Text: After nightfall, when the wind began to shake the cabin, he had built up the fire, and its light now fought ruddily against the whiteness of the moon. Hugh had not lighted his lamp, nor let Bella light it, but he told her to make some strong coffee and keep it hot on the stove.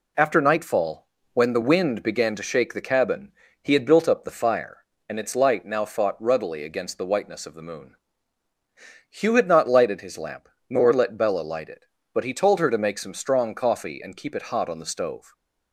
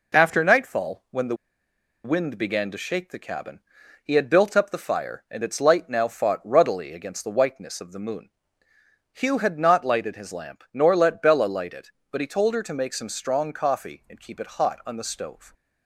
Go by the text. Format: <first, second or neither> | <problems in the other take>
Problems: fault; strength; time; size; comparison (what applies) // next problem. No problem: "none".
first | pauses between "the" and "wind"; noticeable; at 1.3 s; 0.69 s long